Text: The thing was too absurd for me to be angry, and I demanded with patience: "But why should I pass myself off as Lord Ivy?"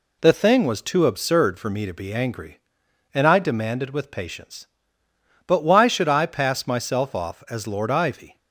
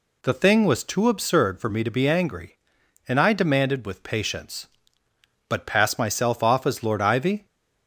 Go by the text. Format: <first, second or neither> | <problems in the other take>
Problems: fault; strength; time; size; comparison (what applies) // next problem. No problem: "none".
first | skips "why should I"; at 5.6 s